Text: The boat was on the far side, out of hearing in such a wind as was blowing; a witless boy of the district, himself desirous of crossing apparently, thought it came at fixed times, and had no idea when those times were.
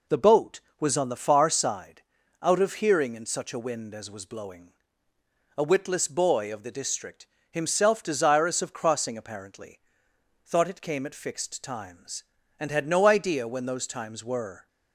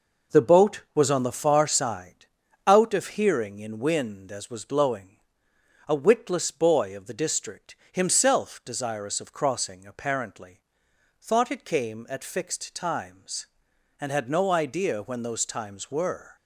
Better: first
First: none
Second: skips "such a"; at 3.7 s

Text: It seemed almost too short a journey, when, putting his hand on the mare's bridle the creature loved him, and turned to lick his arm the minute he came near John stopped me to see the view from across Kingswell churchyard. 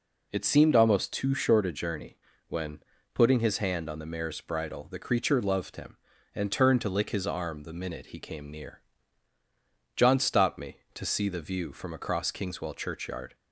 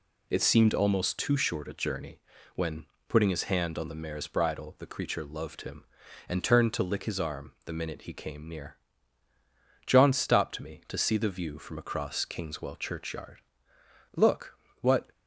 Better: first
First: pauses between "near" and "John"; at 8.7 s; 1.1 s long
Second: pauses between "near" and "John"; at 8.7 s; 1.1 s long // goes on to say "Look what"; noticeable; from 14.1 s on; 0.94 s long

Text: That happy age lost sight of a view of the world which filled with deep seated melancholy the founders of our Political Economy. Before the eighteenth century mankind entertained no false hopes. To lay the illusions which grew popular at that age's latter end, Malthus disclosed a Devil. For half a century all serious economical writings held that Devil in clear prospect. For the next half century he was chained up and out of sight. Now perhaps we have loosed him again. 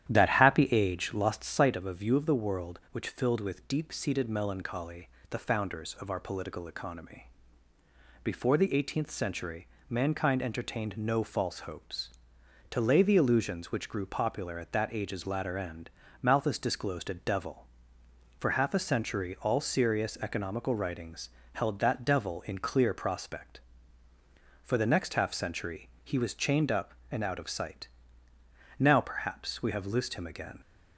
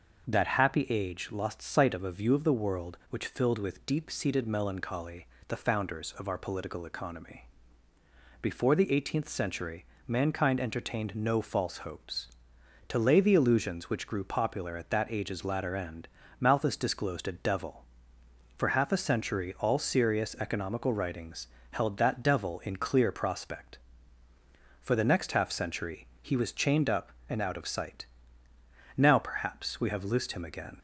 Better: second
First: starts louder than the rest; strong; until 1.6 s; 11 dB // pauses between "melancholy" and "the"; slight; at 5.0 s; 0.22 s long // pauses between "century" and "mankind"; slight; at 9.6 s; 0.20 s long // pauses between "writings" and "held"; slight; at 21.2 s; 0.26 s long // pauses between "century" and "he"; slight; at 25.8 s; 0.16 s long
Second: pauses between "melancholy" and "the"; slight; at 5.2 s; 0.22 s long // pauses between "century" and "mankind"; slight; at 9.8 s; 0.20 s long // pauses between "writings" and "held"; slight; at 21.4 s; 0.26 s long // pauses between "century" and "he"; slight; at 26.0 s; 0.16 s long

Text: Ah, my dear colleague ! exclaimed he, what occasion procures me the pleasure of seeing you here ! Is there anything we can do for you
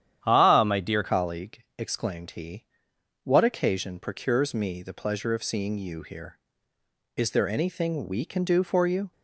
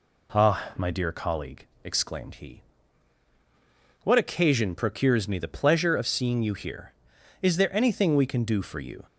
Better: second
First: starts louder than the rest; strong; until 1.2 s; 10 dB // changes voice at "colleague"; from 1.0 s on; 8.1 s long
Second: none

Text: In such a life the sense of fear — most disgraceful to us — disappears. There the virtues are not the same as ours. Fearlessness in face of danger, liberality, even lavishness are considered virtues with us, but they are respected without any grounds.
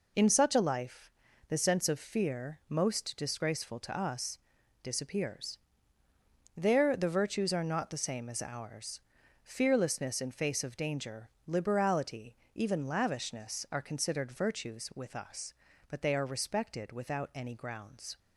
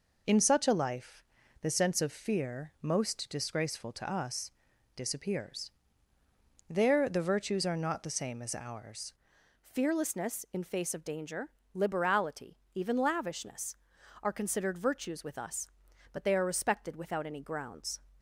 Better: first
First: pauses between "life" and "the"; at 1.1 s; 0.38 s long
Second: pauses between "life" and "the"; at 1.2 s; 0.38 s long // changes voice at "Fearlessness"; from 9.6 s on; 8.4 s long

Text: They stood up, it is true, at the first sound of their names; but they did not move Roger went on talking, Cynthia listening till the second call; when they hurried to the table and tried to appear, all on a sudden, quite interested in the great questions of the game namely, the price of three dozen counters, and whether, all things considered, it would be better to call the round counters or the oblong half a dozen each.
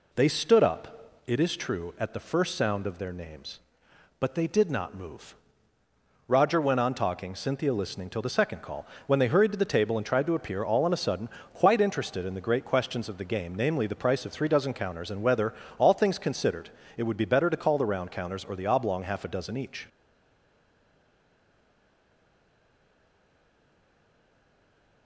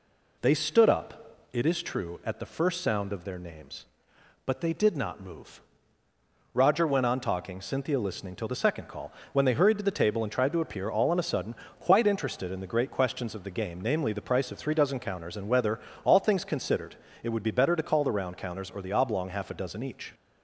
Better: second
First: pauses between "move" and "Roger"; noticeable; at 5.3 s; 0.92 s long // stays silent after the last word; strong; from 19.8 s on; 5.2 s long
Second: pauses between "move" and "Roger"; noticeable; at 5.6 s; 0.92 s long

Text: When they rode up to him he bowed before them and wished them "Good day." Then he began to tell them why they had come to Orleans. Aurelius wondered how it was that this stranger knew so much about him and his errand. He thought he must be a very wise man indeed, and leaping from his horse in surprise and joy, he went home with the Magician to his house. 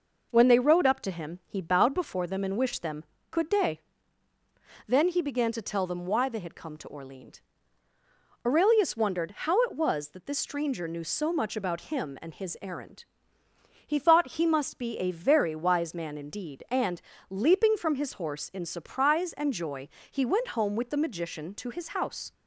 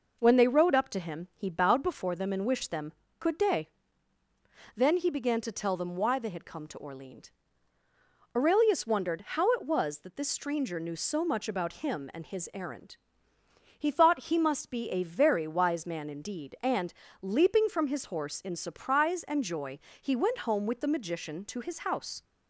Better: neither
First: pauses between "them" and "Good"; slight; at 3.0 s; 0.26 s long // pauses between "and" and "leaping"; slight; at 17.0 s; 0.28 s long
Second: pauses between "them" and "Good"; slight; at 2.9 s; 0.26 s long // pauses between "and" and "leaping"; slight; at 16.9 s; 0.28 s long

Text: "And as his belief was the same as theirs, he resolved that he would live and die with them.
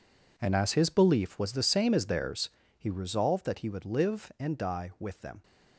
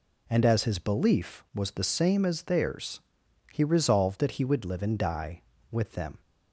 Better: second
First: gets quieter; strong; throughout; 13.5 dB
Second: none

